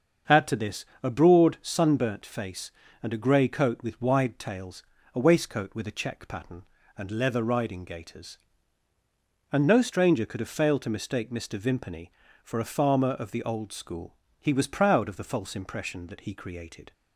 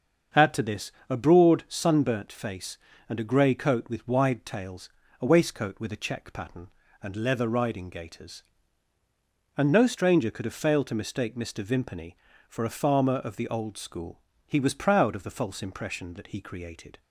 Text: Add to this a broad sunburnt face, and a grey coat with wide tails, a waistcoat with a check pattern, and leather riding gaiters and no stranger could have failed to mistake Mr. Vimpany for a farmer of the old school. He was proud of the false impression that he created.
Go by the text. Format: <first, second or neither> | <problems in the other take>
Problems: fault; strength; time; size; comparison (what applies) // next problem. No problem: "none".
neither | starts louder than the rest; the same in both // pauses between "this" and "a"; slight; the same in both